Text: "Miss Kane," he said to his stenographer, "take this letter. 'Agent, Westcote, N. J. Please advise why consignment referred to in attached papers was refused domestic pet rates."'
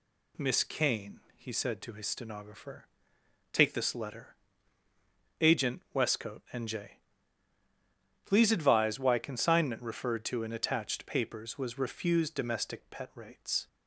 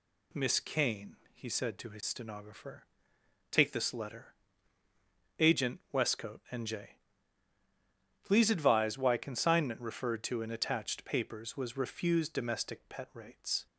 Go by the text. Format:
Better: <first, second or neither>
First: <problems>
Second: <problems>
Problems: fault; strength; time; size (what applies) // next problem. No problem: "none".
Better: neither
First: pauses between "J" and "Please"; strong; at 6.9 s; 1.2 s long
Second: pauses between "J" and "Please"; strong; at 6.9 s; 1.2 s long